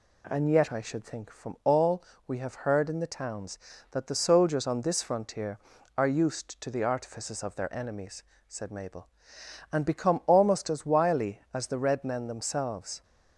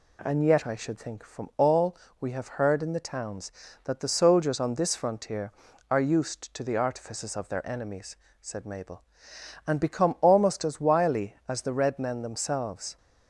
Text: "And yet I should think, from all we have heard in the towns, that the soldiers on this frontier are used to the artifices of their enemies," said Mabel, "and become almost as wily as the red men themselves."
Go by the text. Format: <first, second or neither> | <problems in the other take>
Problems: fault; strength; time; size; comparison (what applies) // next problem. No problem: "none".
neither | pauses between "all" and "we"; slight; the same in both